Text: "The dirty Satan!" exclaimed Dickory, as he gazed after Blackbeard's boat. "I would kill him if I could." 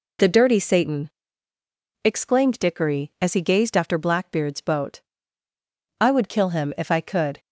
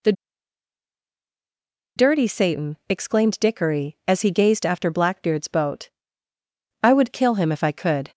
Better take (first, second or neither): first